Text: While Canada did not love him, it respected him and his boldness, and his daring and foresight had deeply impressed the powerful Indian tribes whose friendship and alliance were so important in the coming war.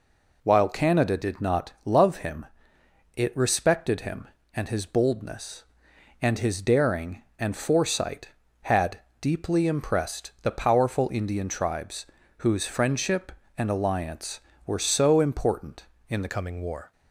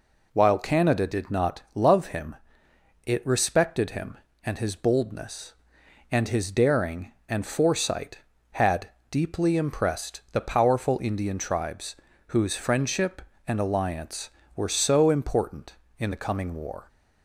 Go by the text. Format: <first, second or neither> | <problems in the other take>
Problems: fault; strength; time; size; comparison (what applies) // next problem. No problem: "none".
second | pauses between "had" and "deeply"; slight; at 8.9 s; 0.20 s long; slight in the second // pauses between "tribes" and "whose"; slight; at 12.0 s; 0.32 s long; slight in the second // changes voice at "coming"; from 16.2 s on; 0.7 s long